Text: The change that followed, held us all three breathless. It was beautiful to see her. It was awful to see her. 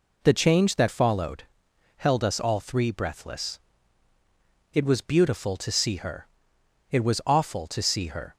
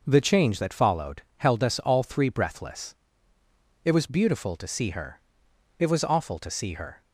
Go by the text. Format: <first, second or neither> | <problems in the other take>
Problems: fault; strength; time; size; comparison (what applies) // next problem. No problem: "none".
neither | none